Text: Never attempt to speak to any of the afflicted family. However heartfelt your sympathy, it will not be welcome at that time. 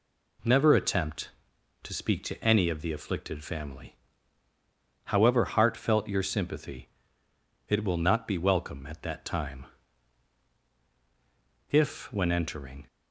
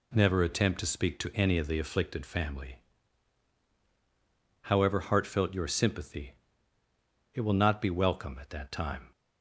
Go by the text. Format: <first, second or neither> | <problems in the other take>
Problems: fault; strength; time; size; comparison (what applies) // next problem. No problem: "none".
second | goes on to say "If when entering"; noticeable; from 11.7 s on; 1.1 s long